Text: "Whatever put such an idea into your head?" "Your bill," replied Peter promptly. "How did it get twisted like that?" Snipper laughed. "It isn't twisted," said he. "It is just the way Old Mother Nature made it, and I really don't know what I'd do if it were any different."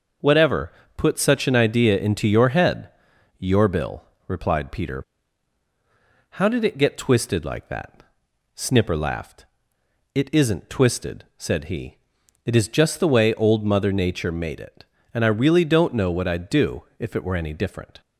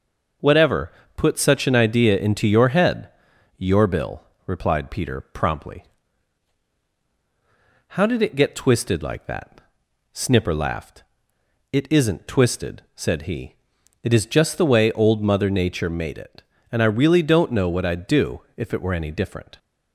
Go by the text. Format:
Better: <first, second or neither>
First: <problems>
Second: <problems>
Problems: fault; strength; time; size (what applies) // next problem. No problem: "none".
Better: second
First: starts louder than the rest; noticeable; until 1.4 s; 6 dB // pauses between "Whatever" and "put"; slight; at 0.7 s; 0.26 s long // skips "promptly"; at 5.6 s // pauses between "do" and "if"; slight; at 16.8 s; 0.16 s long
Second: pauses between "Whatever" and "put"; slight; at 0.9 s; 0.26 s long // pauses between "do" and "if"; slight; at 18.3 s; 0.16 s long